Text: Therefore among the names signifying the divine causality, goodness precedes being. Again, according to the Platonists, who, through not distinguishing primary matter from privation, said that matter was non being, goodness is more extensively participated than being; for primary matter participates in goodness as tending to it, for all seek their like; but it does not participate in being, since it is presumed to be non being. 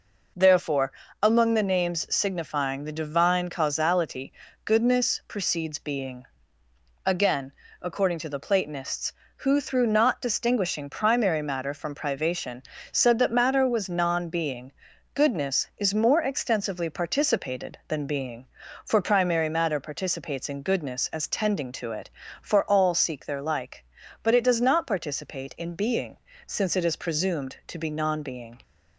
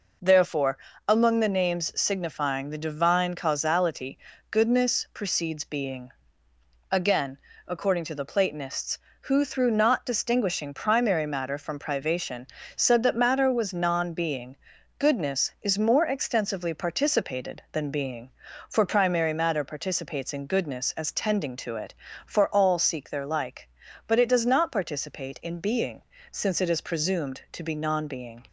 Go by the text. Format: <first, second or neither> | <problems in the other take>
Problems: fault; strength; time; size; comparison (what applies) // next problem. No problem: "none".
neither | pauses between "Therefore" and "among"; slight; the same in both